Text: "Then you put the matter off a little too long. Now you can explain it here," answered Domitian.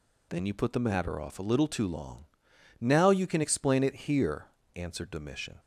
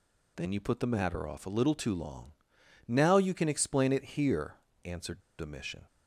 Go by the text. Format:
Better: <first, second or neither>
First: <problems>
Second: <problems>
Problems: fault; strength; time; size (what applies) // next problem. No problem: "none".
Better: first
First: none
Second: pauses between "answered" and "Domitian"; slight; at 5.1 s; 0.19 s long